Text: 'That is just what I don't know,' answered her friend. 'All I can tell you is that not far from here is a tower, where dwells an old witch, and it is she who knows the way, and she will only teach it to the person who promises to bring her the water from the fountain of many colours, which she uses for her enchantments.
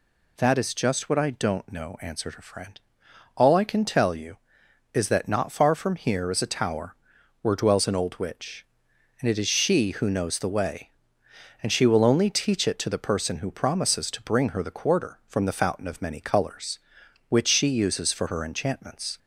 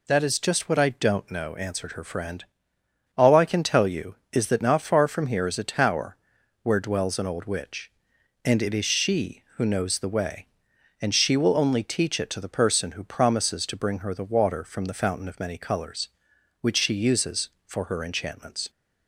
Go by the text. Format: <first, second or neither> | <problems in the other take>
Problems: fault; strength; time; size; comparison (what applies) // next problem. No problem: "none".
second | says "quarter" for "water"; at 14.7 s